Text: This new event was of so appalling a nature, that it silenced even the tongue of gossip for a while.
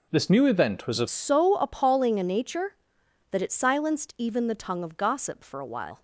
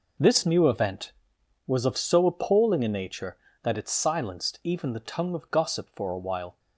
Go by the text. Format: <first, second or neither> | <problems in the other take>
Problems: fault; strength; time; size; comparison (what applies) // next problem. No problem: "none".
second | changes voice at "so"; from 1.0 s on; 5.0 s long